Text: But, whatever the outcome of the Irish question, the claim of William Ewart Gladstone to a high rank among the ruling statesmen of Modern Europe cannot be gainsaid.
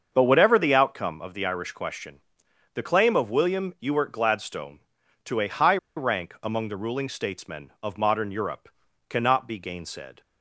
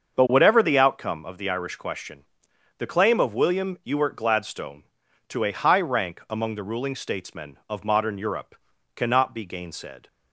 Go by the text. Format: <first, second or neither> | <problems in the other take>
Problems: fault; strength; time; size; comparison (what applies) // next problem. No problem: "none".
second | starts louder than the rest; until 1.1 s; 6.5 dB; also in the second // pauses between "high" and "rank"; slight; at 5.7 s; 0.19 s long // pauses between "Europe" and "cannot"; at 8.6 s; 0.40 s long; also in the second